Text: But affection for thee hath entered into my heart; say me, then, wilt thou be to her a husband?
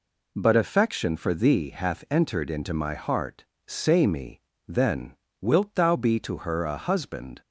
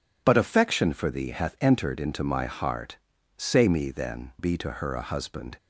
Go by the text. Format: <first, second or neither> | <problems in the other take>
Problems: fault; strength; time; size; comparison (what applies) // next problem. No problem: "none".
first | skips "wilt thou"; at 4.3 s